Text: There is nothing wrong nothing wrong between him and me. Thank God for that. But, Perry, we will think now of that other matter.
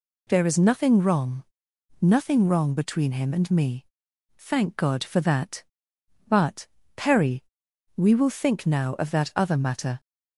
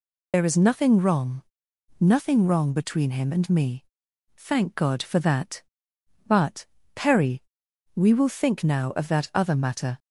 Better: first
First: pauses between "wrong" and "nothing"; noticeable; at 1.4 s; 0.56 s long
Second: loses the start of "There"; at 0.3 s; 60 ms // pauses between "wrong" and "nothing"; noticeable; at 1.4 s; 0.56 s long

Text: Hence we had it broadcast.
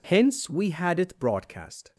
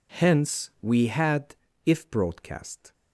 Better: first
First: none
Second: says "if" for "it"; at 1.8 s

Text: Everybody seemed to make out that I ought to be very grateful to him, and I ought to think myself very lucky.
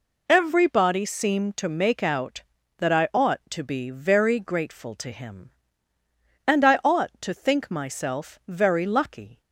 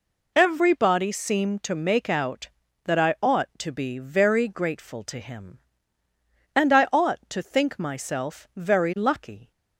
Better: neither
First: none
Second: none

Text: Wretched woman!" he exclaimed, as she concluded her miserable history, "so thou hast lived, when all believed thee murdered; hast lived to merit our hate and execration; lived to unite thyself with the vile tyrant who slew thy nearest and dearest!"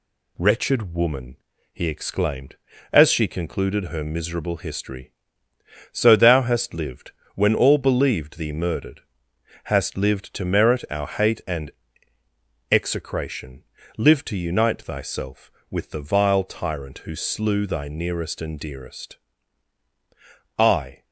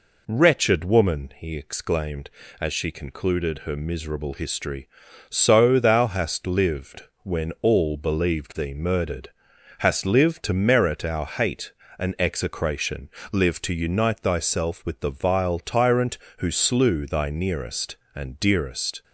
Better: second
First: pauses between "and" and "execration"; at 11.7 s; 1.0 s long // goes on to say "I"; slight; from 20.5 s on; 0.46 s long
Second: none

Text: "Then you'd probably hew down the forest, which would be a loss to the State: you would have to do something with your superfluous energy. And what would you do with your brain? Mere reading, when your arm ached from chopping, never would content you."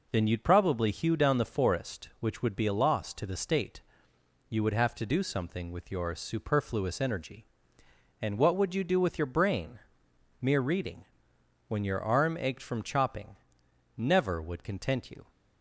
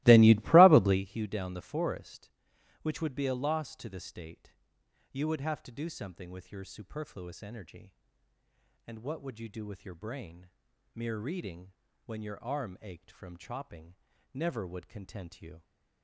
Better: first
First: none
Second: starts louder than the rest; strong; until 1.0 s; 20 dB

